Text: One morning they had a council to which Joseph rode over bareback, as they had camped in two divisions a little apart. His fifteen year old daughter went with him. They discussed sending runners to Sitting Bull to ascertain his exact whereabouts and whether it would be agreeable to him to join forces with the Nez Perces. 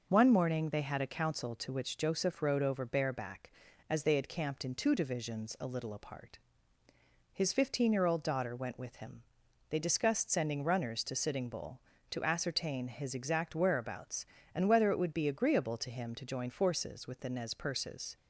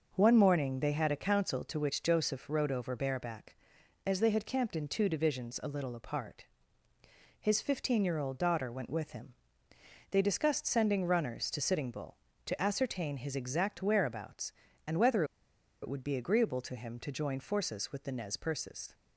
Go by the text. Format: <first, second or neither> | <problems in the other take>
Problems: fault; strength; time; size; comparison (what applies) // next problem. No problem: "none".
first | pauses between "whether" and "it"; noticeable; at 15.2 s; 0.58 s long